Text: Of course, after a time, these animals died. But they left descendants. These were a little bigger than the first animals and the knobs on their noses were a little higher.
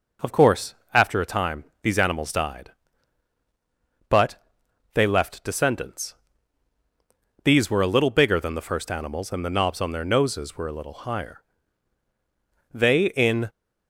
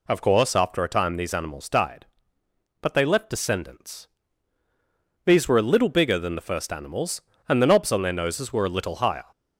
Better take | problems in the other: second | pauses between "But" and "they"; noticeable; at 4.3 s; 0.58 s long // goes on to say "They in"; noticeable; from 12.7 s on; 0.76 s long

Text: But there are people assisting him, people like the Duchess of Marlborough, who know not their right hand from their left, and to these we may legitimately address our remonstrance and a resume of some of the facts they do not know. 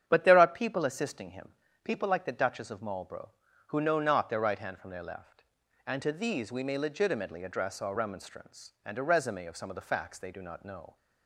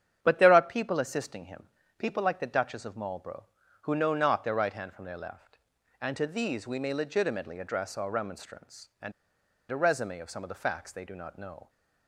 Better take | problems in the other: first | starts louder than the rest; strong; until 1.2 s; 9 dB; strong in the first // pauses between "and" and "a"; noticeable; at 9.1 s; 0.59 s long

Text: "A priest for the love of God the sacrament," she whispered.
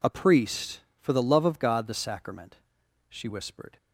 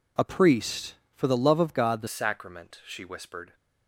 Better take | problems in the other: first | changes voice at "sacrament"; from 2.0 s on; 1.5 s long

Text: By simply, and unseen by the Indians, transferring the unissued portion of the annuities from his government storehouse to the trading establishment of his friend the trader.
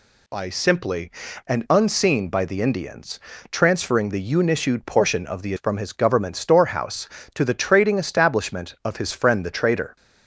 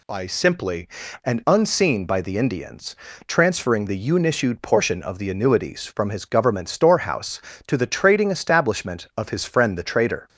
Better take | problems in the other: second | skips "annuities"; at 5.5 s

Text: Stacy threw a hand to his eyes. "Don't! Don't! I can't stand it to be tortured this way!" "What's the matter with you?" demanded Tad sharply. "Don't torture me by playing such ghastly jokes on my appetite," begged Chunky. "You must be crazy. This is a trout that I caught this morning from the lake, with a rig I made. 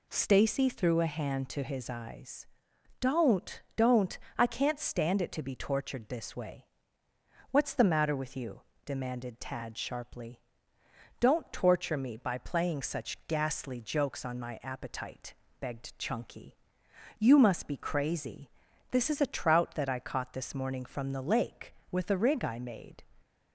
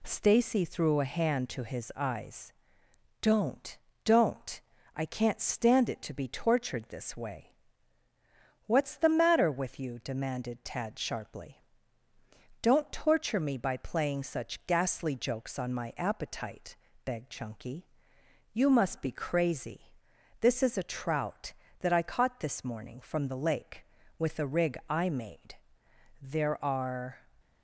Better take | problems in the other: first | goes on to say "There are"; noticeable; from 26.2 s on; 0.98 s long

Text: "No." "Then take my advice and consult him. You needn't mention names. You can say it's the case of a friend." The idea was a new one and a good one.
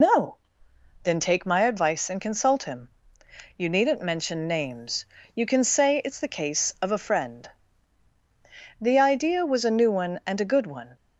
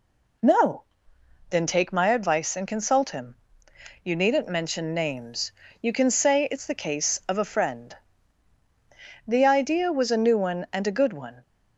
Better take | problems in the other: second | loses the start of "No"; at 0.0 s; 70 ms

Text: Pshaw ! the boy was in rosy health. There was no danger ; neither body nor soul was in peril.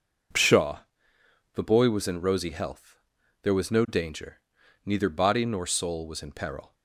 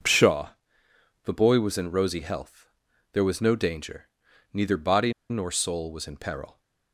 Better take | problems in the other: first | pauses between "body" and "nor"; slight; at 5.1 s; 0.18 s long

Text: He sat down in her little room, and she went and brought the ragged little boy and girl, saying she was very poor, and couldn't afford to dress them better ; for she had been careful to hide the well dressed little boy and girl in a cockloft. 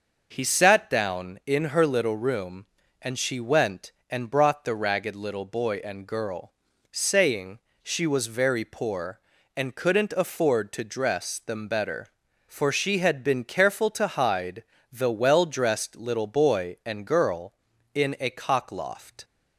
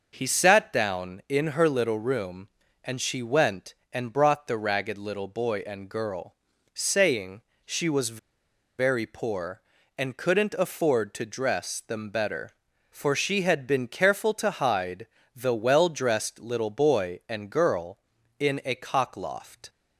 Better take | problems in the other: first | pauses between "saying" and "she"; slight; at 7.4 s; 0.24 s long; slight in the first // pauses between "was" and "very"; noticeable; at 8.1 s; 0.59 s long // pauses between "hide" and "the"; slight; at 15.0 s; 0.30 s long; slight in the first

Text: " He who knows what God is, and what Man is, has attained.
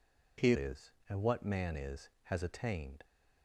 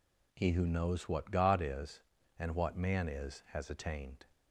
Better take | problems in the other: second | skips "who knows what God"; at 0.5 s

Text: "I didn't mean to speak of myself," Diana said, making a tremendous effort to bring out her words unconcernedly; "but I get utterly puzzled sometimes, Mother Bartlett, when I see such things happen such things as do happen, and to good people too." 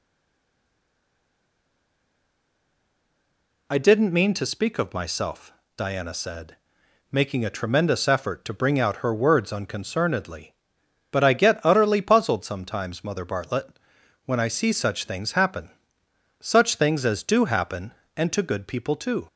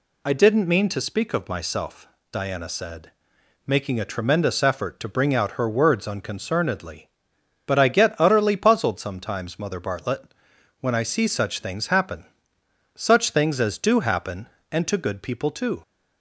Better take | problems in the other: second | stays silent before the first word; strong; until 3.6 s; 3.6 s long // pauses between "happen" and "such"; noticeable; at 15.6 s; 0.70 s long; noticeable in the second

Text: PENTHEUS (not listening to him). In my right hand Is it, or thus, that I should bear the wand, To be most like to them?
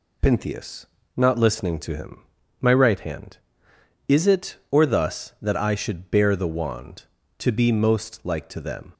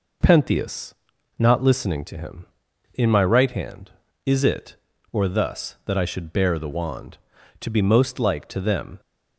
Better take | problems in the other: second | skips "In"; at 2.4 s

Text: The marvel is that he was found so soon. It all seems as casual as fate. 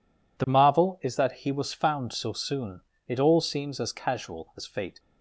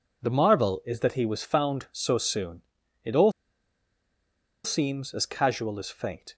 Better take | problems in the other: first | pauses between "all" and "seems"; strong; at 3.3 s; 1.3 s long

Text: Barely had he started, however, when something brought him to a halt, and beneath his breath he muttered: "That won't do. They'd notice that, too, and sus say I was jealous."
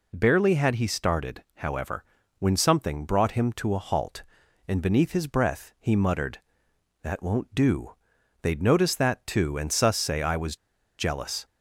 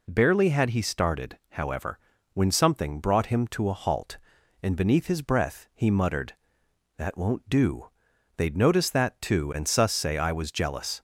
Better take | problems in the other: second | pauses between "was" and "jealous"; at 10.5 s; 0.43 s long

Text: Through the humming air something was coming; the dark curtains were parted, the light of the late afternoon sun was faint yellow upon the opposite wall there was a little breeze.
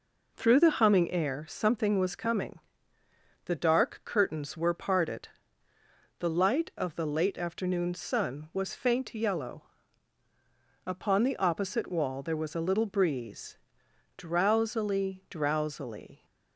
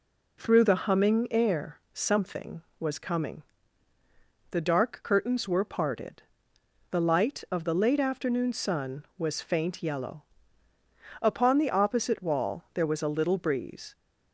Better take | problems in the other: second | pauses between "yellow" and "upon"; at 9.6 s; 1.2 s long; noticeable in the second // goes on to say "Drowsily drowsily"; strong; from 14.1 s on; 2.0 s long

